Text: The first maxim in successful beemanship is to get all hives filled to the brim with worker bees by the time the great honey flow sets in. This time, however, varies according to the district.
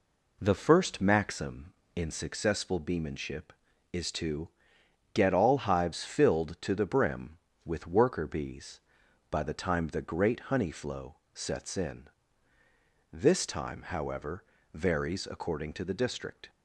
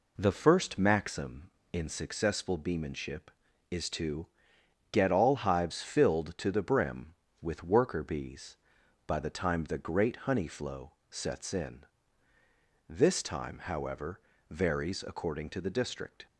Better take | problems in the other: neither | pauses between "to" and "get"; noticeable; the same in both // pauses between "flow" and "sets"; slight; the same in both

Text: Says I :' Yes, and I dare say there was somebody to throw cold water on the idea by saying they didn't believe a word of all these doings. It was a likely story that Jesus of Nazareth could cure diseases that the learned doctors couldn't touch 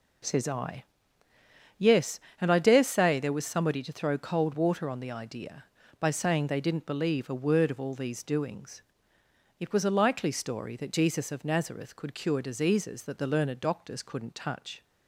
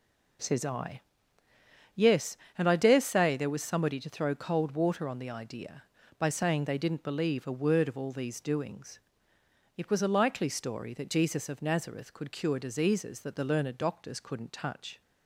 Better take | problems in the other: neither | none

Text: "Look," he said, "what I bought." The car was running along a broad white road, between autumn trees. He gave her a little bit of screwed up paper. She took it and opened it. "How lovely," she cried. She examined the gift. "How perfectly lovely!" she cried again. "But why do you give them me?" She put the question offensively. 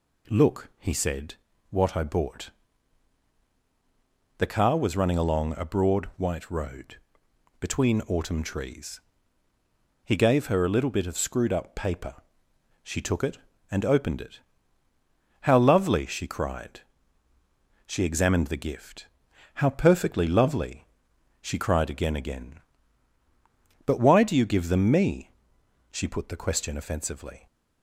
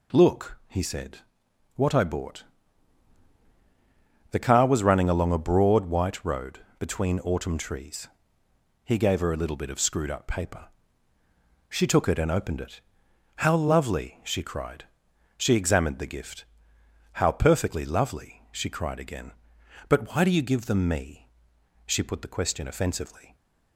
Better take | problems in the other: second | says "again" twice; at 22.1 s

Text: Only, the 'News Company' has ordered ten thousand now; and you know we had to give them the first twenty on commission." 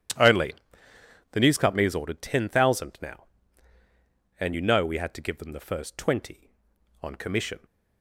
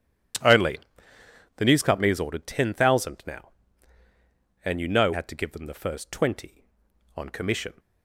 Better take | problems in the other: first | skips "we"; at 5.1 s

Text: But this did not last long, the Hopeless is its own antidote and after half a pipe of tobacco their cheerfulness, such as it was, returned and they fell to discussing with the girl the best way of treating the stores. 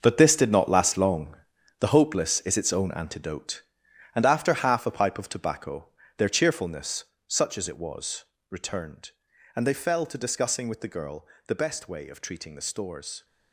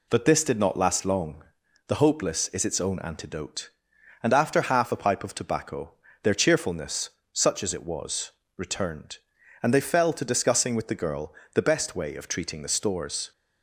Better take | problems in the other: second | gets quieter; strong; throughout; 11.5 dB // pauses between "tobacco" and "their"; slight; at 5.8 s; 0.30 s long; slight in the second // pauses between "girl" and "the"; slight; at 11.2 s; 0.20 s long; slight in the second

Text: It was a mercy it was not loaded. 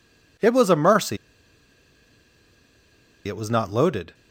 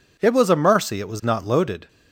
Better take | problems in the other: second | pauses between "mercy" and "it"; strong; at 1.1 s; 2.1 s long

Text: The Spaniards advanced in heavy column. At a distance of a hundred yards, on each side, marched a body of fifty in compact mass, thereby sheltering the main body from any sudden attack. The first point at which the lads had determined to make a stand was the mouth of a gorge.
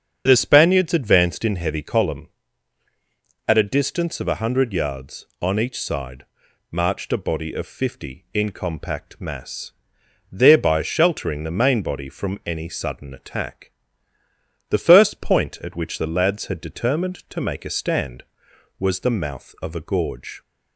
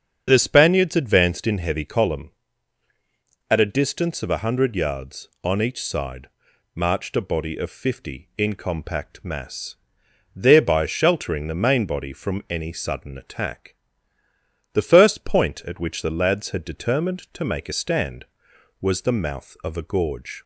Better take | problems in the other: neither | starts louder than the rest; strong; the same in both

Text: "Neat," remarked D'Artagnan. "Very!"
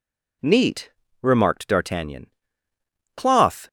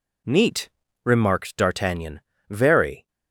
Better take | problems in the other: second | says "Cloth" for "Very"; at 3.1 s

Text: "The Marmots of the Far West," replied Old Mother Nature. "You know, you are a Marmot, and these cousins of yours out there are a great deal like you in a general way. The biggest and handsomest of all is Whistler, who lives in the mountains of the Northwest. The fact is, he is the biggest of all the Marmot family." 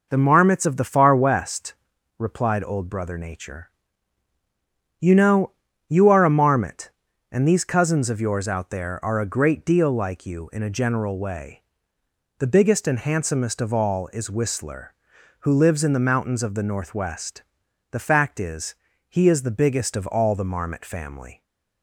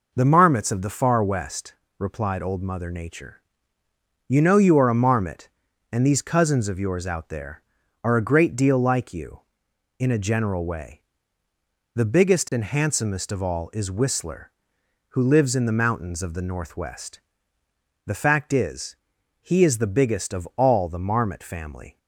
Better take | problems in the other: second | says "Brother" for "Mother"; at 2.8 s

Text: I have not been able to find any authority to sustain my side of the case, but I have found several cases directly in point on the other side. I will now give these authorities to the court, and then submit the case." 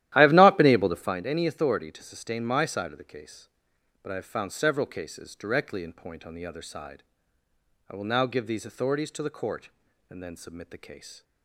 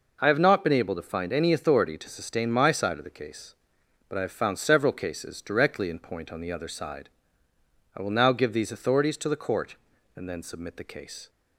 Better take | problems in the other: second | starts louder than the rest; strong; until 1.2 s; 13.5 dB

